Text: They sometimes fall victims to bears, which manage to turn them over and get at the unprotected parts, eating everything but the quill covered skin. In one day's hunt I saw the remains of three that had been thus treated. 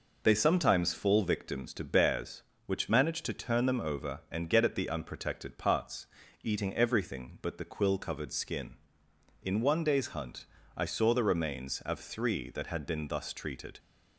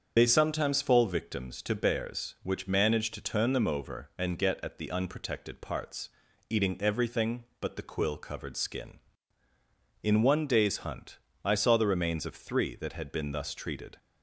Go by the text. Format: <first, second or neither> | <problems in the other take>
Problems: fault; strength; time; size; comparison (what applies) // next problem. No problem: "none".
first | loses the start of "They"; at 0.1 s; 55 ms // starts louder than the rest; strong; until 1.1 s; 7 dB // pauses between "hunt" and "I"; slight; at 11.1 s; 0.26 s long; slight in the first